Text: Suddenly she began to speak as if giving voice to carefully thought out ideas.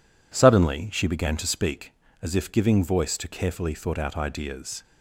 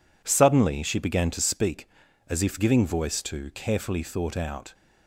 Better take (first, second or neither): first